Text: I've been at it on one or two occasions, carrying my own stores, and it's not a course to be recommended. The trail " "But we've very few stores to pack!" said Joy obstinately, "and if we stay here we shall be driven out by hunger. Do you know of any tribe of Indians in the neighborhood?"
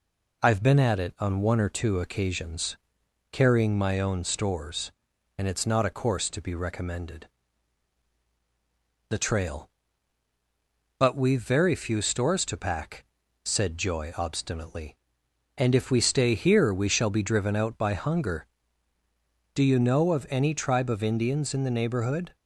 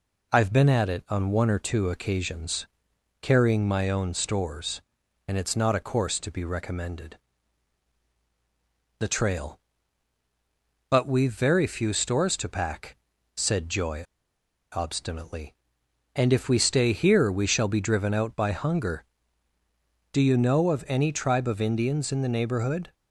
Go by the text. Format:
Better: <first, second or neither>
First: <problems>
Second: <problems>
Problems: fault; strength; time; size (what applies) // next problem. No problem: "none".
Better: first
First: none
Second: pauses between "Joy" and "obstinately"; noticeable; at 14.0 s; 0.68 s long